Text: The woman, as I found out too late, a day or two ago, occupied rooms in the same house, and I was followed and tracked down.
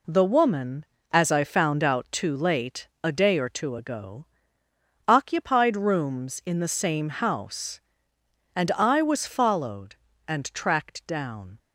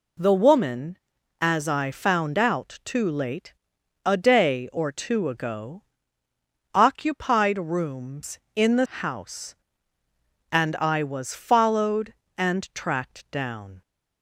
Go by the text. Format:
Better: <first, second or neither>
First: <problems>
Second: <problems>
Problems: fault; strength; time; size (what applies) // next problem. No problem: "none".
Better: first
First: none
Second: skips "same"; at 8.8 s